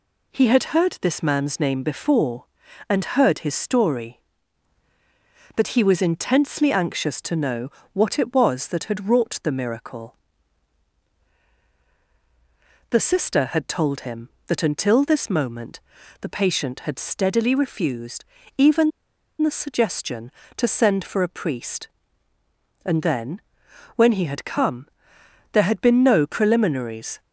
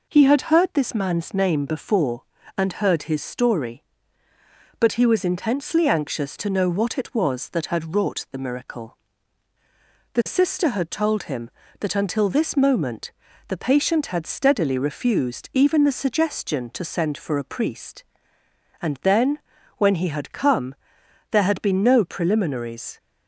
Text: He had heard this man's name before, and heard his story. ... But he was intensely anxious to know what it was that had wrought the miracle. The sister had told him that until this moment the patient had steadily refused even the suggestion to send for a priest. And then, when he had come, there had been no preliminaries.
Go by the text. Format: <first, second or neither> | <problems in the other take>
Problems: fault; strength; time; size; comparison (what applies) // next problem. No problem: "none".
second | pauses between "know" and "what"; slight; at 7.6 s; 0.24 s long // pauses between "moment" and "the"; at 15.8 s; 0.40 s long; slight in the second // pauses between "refused" and "even"; slight; at 18.2 s; 0.32 s long // pauses between "even" and "the"; noticeable; at 18.9 s; 0.51 s long